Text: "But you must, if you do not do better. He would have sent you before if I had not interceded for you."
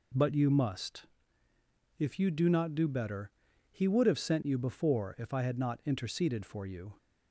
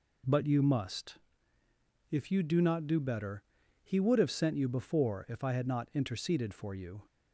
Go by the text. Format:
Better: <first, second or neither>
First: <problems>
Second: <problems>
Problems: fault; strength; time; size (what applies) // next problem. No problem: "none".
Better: neither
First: none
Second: none